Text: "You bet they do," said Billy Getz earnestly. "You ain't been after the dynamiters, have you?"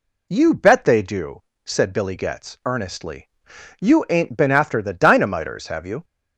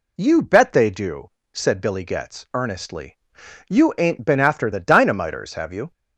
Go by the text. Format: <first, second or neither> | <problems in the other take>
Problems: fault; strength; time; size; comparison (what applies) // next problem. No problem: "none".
neither | none